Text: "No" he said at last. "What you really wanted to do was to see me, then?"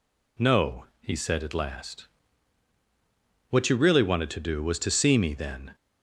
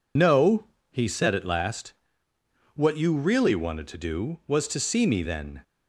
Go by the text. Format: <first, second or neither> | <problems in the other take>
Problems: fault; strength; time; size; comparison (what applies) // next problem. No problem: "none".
first | loses the start of "No"; at 0.1 s; 90 ms // pauses between "No" and "he"; slight; at 0.6 s; 0.20 s long; slight in the first